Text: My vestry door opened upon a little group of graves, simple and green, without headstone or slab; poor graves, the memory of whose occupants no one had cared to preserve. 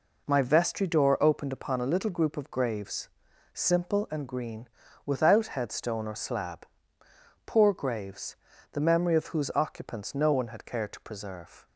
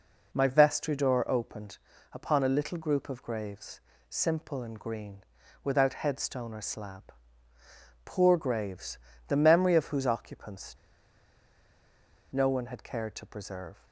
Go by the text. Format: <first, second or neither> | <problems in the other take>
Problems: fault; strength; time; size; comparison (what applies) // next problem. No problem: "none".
first | pauses between "opened" and "upon"; slight; at 1.7 s; 0.36 s long // pauses between "occupants" and "no"; strong; at 10.7 s; 1.6 s long